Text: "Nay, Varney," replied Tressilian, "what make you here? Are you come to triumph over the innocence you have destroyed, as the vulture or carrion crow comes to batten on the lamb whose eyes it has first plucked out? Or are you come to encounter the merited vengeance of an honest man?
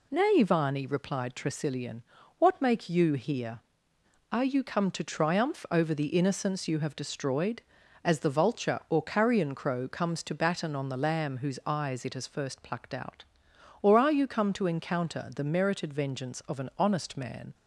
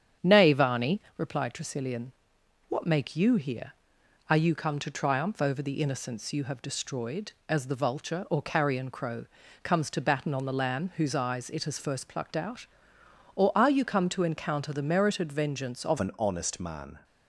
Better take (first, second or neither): first